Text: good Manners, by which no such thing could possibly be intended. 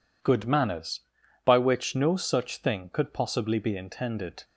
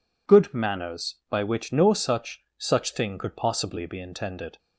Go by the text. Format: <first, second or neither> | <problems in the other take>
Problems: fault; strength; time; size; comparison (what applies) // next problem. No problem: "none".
first | says "such" twice; at 2.5 s